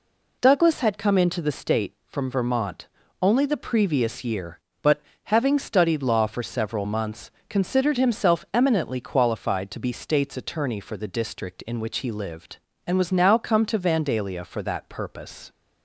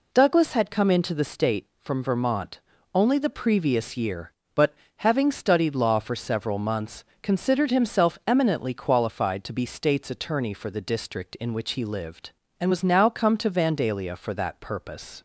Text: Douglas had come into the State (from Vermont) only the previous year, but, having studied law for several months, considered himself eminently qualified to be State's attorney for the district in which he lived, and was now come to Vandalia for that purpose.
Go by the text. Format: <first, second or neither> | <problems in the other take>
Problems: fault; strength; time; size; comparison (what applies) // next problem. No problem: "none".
neither | none